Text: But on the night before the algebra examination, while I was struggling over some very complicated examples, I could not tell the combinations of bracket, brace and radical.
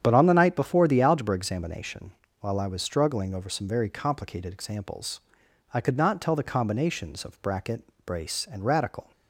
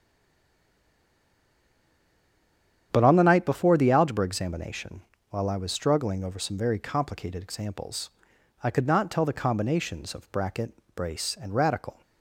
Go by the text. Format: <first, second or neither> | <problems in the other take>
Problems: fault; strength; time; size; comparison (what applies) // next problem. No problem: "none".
first | stays silent before the first word; strong; until 2.9 s; 2.9 s long // starts louder than the rest; strong; until 3.9 s; 8.5 dB; strong in the first